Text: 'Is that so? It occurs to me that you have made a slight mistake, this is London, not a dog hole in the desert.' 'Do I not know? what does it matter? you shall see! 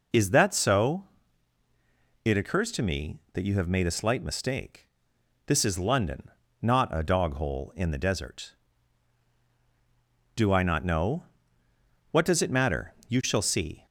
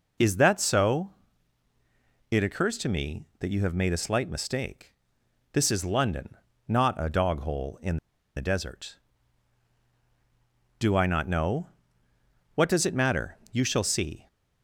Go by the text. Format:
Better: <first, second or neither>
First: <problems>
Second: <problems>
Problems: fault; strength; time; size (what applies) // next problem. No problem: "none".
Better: first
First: none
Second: pauses between "in" and "the"; at 7.9 s; 0.38 s long